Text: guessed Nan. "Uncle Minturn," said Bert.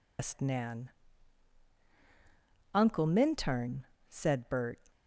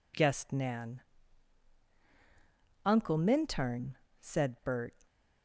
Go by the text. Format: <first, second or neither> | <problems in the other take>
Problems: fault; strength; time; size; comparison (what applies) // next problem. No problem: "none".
second | loses the start of "guessed"; at 0.1 s; 160 ms